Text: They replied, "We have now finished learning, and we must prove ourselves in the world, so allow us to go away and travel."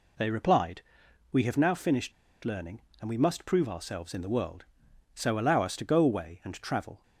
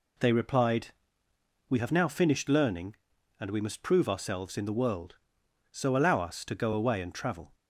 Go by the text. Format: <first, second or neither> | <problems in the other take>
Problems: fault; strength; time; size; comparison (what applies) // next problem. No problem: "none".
second | pauses between "finished" and "learning"; slight; at 2.1 s; 0.32 s long